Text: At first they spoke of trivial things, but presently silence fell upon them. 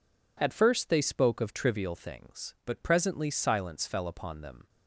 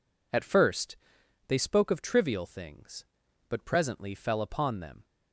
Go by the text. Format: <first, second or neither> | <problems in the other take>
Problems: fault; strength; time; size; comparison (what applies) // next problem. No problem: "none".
first | pauses between "first" and "they"; noticeable; at 0.9 s; 0.52 s long // skips "silence"; at 4.1 s